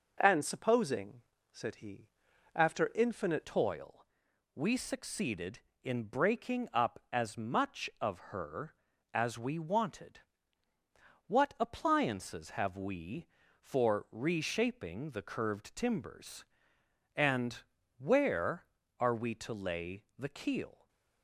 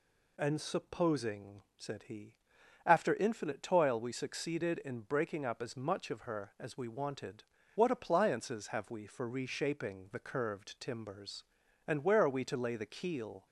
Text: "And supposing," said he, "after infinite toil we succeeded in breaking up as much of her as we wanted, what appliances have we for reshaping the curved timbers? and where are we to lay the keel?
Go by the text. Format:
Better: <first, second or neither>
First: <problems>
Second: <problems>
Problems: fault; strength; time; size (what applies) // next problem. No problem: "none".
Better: second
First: changes voice at "toil"; from 3.4 s on; 17.4 s long // pauses between "toil" and "we"; noticeable; at 4.0 s; 0.52 s long // pauses between "of" and "her"; slight; at 8.1 s; 0.16 s long // pauses between "and" and "where"; slight; at 17.6 s; 0.34 s long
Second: none